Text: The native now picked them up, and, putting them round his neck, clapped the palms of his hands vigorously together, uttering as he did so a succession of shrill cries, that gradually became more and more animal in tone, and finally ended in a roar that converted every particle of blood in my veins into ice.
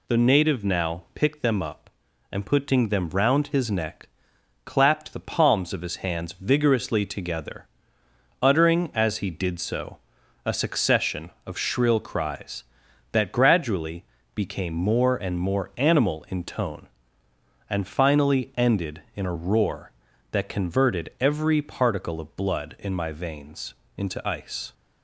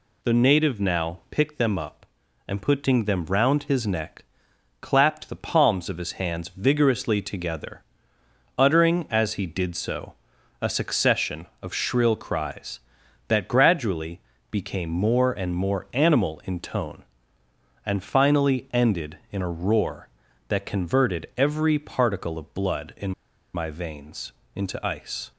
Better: first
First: pauses between "so" and "a"; noticeable; at 9.9 s; 0.48 s long // pauses between "gradually" and "became"; slight; at 14.0 s; 0.30 s long // pauses between "veins" and "into"; slight; at 23.7 s; 0.22 s long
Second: pauses between "so" and "a"; noticeable; at 10.1 s; 0.48 s long // pauses between "gradually" and "became"; slight; at 14.2 s; 0.30 s long // pauses between "in" and "my"; at 23.1 s; 0.43 s long // pauses between "veins" and "into"; slight; at 24.3 s; 0.22 s long

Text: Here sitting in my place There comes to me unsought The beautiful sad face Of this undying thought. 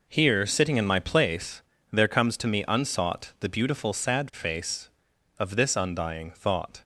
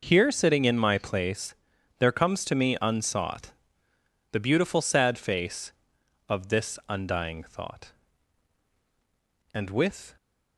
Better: first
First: pauses between "place" and "There"; slight; at 1.6 s; 0.30 s long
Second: pauses between "place" and "There"; at 1.5 s; 0.44 s long // pauses between "unsought" and "The"; noticeable; at 3.5 s; 0.80 s long // goes on to say "And with"; noticeable; from 9.5 s on; 0.62 s long

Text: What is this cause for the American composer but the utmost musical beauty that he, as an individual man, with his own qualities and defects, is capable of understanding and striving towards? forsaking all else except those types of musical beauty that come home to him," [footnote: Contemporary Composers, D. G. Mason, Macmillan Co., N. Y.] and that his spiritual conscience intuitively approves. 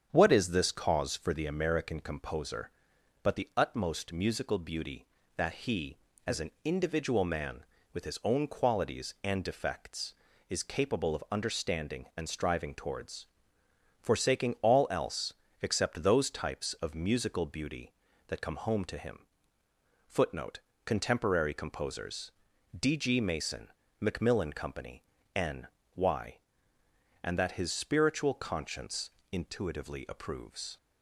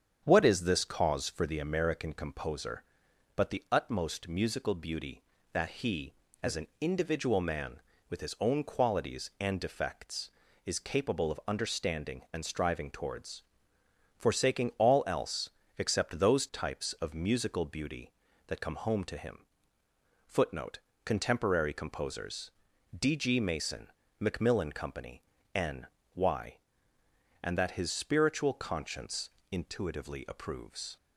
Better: neither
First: starts louder than the rest; strong; until 1.1 s; 8 dB // pauses between "else" and "except"; slight; at 15.3 s; 0.28 s long // pauses between "N" and "Y"; slight; at 25.6 s; 0.30 s long // pauses between "conscience" and "intuitively"; slight; at 29.1 s; 0.22 s long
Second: starts louder than the rest; strong; until 1.2 s; 8 dB // pauses between "else" and "except"; slight; at 15.4 s; 0.28 s long // pauses between "N" and "Y"; slight; at 25.8 s; 0.30 s long // pauses between "conscience" and "intuitively"; slight; at 29.3 s; 0.22 s long

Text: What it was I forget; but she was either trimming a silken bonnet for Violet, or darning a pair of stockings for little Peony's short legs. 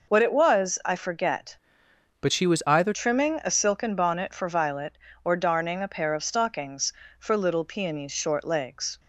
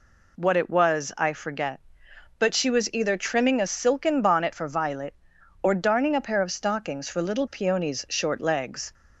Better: second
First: changes voice from "but" to "either"; from 2.2 to 2.9 s; 0.7 s long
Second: none

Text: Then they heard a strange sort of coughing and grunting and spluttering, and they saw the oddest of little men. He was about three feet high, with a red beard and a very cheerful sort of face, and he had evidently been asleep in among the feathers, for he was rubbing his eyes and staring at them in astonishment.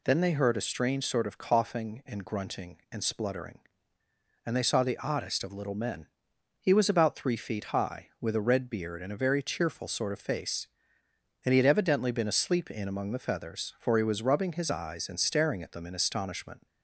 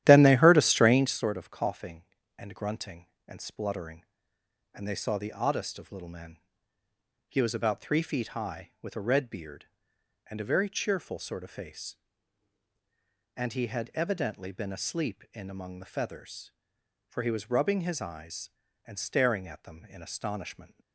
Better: first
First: none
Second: starts louder than the rest; strong; until 1.3 s; 12 dB

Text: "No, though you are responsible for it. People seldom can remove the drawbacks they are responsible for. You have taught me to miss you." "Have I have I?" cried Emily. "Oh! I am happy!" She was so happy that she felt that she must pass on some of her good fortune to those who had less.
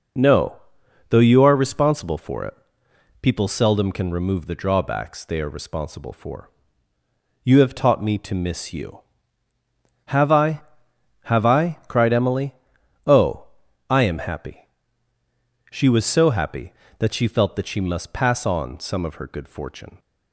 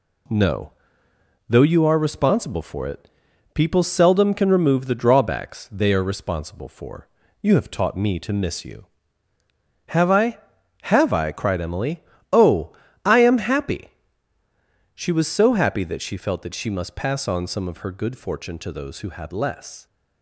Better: second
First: stops before "to those who had less"; at 19.9 s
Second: none

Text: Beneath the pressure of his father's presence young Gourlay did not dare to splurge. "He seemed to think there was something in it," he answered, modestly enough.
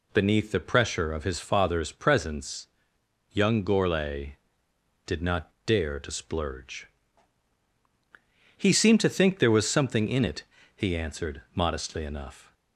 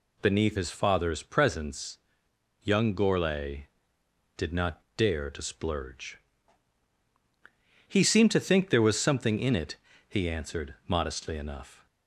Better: first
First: pauses between "presence" and "young"; noticeable; at 2.6 s; 0.66 s long // pauses between "not" and "dare"; slight; at 5.5 s; 0.16 s long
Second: skips "the pressure of"; at 0.5 s // pauses between "presence" and "young"; noticeable; at 1.9 s; 0.66 s long // pauses between "not" and "dare"; slight; at 4.8 s; 0.16 s long

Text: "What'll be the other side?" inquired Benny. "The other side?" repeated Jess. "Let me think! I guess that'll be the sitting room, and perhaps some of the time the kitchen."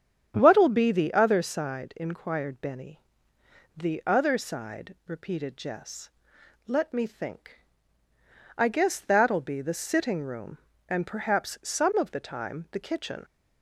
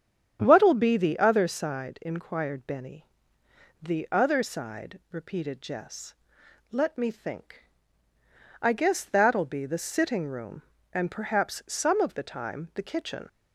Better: neither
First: starts louder than the rest; strong; until 1.3 s; 8.5 dB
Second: starts louder than the rest; strong; until 1.4 s; 8.5 dB

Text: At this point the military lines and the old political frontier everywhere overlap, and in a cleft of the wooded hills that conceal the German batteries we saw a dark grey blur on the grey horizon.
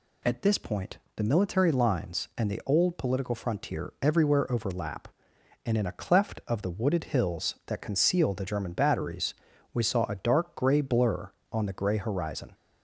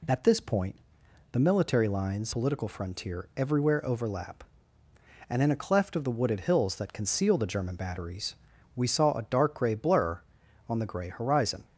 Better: first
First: pauses between "point" and "the"; slight; at 0.9 s; 0.18 s long // pauses between "batteries" and "we"; at 9.3 s; 0.40 s long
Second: pauses between "point" and "the"; noticeable; at 0.7 s; 0.56 s long // skips "and the old"; at 2.3 s // pauses between "batteries" and "we"; at 8.3 s; 0.40 s long

